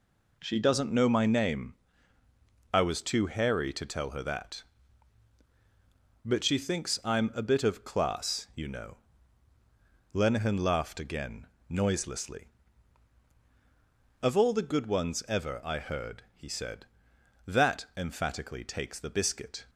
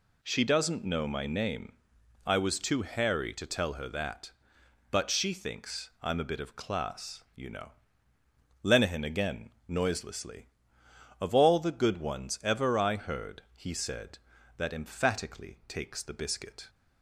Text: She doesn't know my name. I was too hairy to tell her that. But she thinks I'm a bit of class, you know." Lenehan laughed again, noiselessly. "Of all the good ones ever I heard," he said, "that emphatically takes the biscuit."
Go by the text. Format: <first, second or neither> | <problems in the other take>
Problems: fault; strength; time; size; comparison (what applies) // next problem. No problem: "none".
first | skips "laughed"; at 9.0 s